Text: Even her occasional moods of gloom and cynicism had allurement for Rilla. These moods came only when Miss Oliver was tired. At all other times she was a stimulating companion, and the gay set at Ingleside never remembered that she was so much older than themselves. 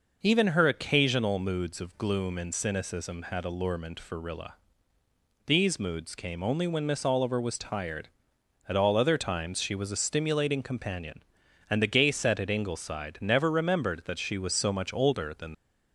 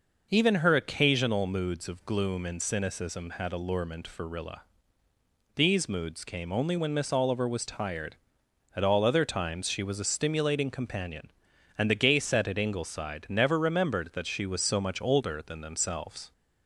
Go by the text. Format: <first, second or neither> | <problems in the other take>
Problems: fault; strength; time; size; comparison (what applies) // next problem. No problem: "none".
second | stops before "themselves"; at 15.5 s